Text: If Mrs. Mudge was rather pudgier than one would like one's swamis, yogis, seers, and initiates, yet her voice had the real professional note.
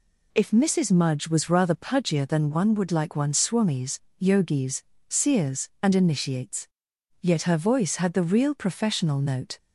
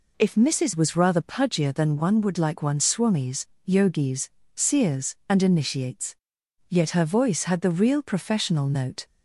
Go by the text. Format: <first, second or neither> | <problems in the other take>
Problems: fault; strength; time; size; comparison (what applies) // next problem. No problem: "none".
first | skips "Mudge"; at 0.7 s